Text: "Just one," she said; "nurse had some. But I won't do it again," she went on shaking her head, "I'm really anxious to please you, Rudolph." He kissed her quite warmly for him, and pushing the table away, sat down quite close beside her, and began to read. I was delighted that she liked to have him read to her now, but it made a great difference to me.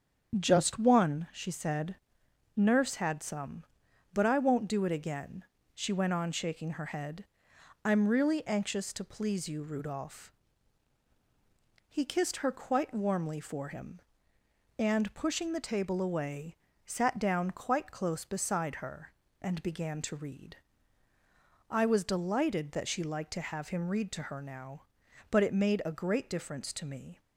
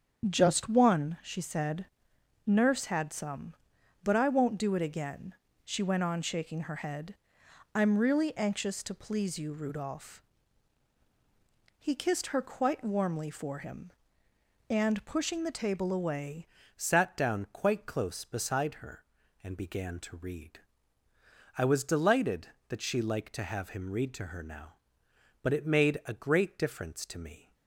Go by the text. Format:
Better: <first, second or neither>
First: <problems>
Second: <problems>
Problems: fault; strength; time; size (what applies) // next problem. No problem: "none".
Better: first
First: starts louder than the rest; strong; until 1.4 s; 7.5 dB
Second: starts louder than the rest; strong; until 1.2 s; 7.5 dB // changes voice at "sat"; from 16.7 s on; 10.8 s long